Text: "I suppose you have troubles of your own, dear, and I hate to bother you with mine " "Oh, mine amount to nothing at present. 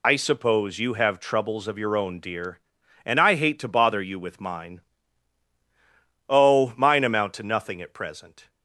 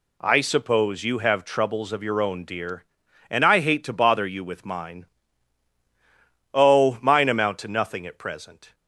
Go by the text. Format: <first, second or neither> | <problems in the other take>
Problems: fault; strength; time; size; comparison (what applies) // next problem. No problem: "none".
second | loses the start of "I"; at 0.0 s; 95 ms